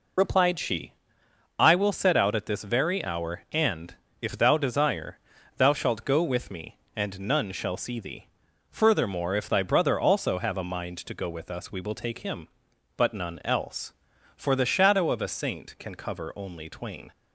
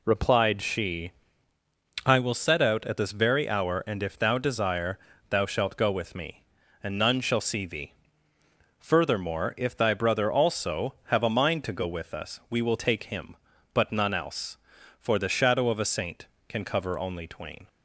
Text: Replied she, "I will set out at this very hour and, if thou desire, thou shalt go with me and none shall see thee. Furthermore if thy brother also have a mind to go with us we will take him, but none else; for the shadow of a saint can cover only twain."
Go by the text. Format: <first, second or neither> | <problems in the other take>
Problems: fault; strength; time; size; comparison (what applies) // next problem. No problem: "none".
second | loses the start of "Replied"; at 0.1 s; 30 ms